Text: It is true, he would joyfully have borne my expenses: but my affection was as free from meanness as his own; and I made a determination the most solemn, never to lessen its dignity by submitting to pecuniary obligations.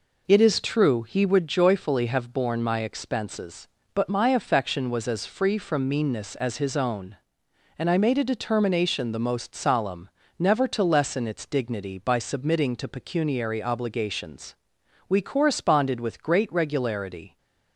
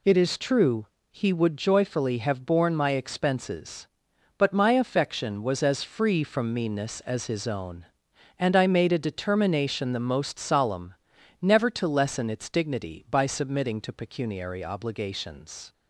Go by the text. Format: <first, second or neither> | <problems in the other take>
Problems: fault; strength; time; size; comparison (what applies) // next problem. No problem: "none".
second | goes on to say "We corresponded with great regularity"; strong; from 15.0 s on; 2.2 s long